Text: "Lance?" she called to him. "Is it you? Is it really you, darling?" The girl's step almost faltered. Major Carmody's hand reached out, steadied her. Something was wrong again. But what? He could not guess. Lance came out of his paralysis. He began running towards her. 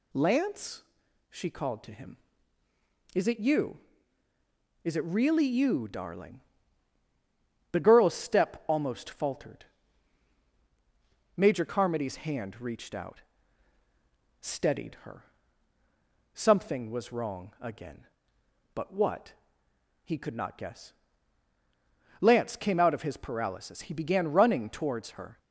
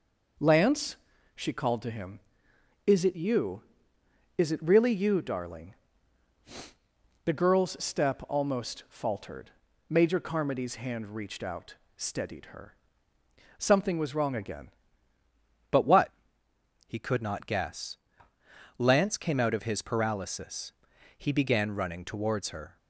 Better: first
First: none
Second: changes voice at "But"; from 15.7 s on; 7.0 s long

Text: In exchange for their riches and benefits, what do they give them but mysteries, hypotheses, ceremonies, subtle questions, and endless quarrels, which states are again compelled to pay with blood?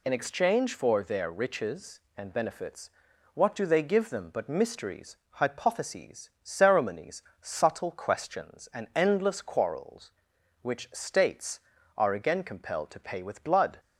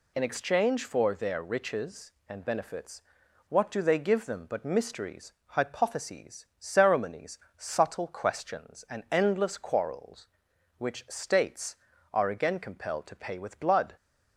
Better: neither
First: none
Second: none

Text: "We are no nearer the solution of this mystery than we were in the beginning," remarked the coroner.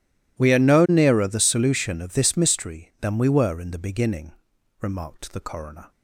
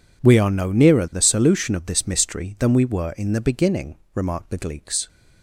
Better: first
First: none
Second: says "gleeks" for "coroner"; at 4.5 s

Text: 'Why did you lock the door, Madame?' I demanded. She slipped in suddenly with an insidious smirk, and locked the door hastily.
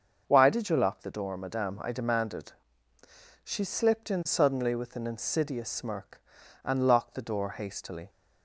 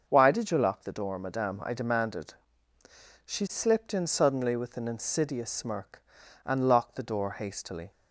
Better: neither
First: starts louder than the rest; until 1.2 s; 6.5 dB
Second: starts louder than the rest; until 1.0 s; 6.5 dB

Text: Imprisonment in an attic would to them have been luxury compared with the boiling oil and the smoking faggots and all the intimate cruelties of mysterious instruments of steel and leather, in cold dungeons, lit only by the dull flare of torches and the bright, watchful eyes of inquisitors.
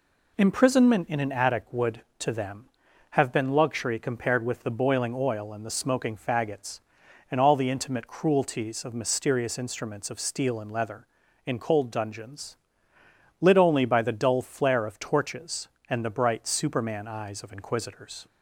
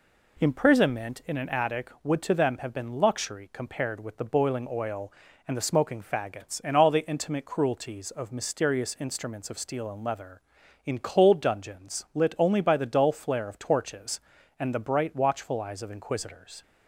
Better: second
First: says "superman" for "watchful"; at 16.4 s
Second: none

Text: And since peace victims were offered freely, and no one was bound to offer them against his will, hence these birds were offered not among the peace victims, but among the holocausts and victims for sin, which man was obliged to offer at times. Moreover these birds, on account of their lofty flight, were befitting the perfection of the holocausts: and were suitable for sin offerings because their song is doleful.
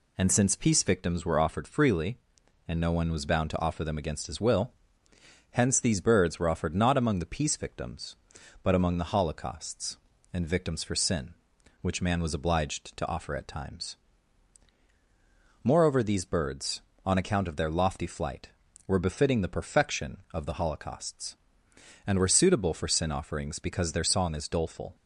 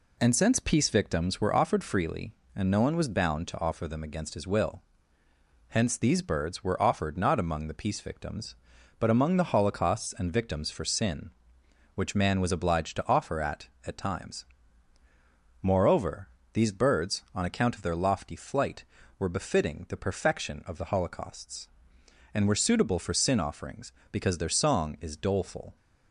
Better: first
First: none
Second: says "at" twice; at 13.8 s // pauses between "Moreover" and "these"; slight; at 16.2 s; 0.26 s long

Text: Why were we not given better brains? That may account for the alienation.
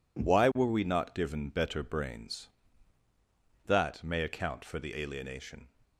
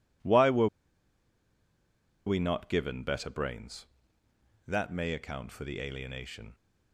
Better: first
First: none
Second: pauses between "were" and "we"; strong; at 0.6 s; 1.5 s long

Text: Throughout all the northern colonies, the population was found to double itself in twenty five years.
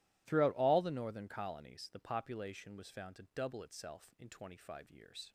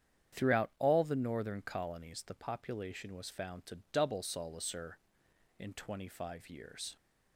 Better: first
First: none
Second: starts louder than the rest; strong; until 1.4 s; 8.5 dB // says "solacer" for "itself"; at 4.2 s

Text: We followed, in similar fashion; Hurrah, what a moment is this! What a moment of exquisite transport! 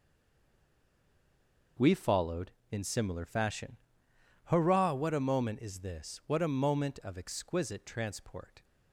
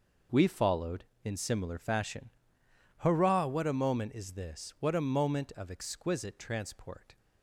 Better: second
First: stays silent before the first word; noticeable; until 1.7 s; 1.7 s long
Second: none

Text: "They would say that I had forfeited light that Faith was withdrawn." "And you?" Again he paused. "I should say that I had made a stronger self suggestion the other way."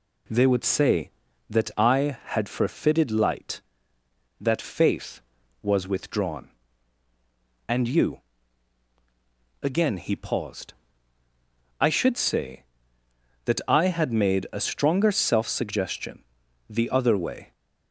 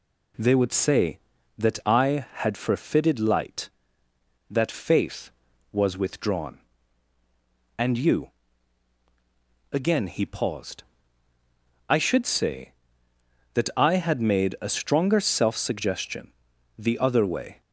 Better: neither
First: pauses between "suggestion" and "the"; at 16.2 s; 0.44 s long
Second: pauses between "suggestion" and "the"; at 16.3 s; 0.44 s long

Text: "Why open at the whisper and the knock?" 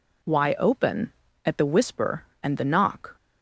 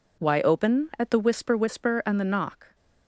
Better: first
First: none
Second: says "whisper" twice; at 1.5 s

